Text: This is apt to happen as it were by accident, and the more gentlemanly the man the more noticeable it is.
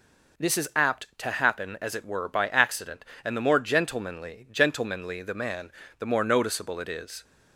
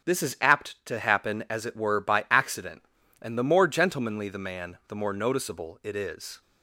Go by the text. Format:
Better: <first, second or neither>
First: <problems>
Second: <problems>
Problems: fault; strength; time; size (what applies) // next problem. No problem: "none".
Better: second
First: says "gentlemanly" twice; at 4.5 s // pauses between "man" and "the"; slight; at 5.7 s; 0.26 s long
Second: none